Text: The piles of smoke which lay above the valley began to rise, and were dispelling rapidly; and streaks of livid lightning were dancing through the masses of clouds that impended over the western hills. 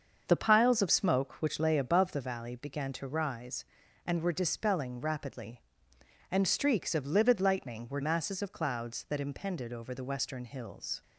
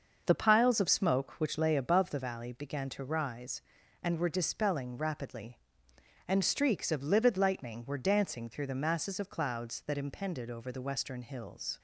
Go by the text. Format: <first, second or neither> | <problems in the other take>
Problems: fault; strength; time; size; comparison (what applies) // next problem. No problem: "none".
second | starts louder than the rest; until 1.2 s; 6.5 dB; also in the second // skips "dancing through the"; at 8.0 s